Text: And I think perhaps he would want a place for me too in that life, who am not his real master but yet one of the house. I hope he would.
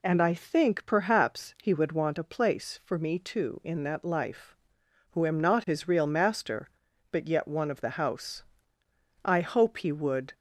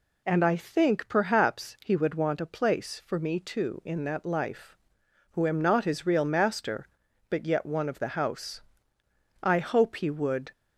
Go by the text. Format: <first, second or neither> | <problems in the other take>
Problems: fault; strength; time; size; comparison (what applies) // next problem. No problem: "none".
neither | none